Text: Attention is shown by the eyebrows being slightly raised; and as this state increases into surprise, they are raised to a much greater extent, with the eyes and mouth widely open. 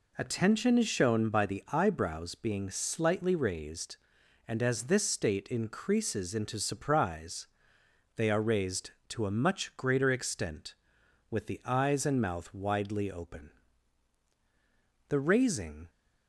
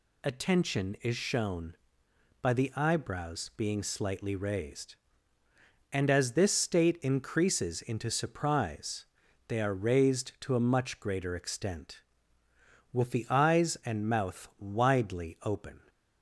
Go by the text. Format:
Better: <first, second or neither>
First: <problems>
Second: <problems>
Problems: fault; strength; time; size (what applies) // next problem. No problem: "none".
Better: second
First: goes on to say "The raising"; noticeable; from 15.0 s on; 0.78 s long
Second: none